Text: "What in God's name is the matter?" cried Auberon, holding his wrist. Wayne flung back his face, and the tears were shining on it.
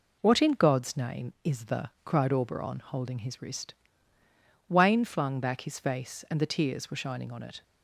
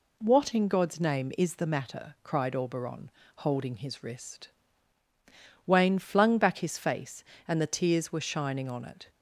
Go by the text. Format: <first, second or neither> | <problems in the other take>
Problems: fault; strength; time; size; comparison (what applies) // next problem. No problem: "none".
second | skips "matter"; at 1.9 s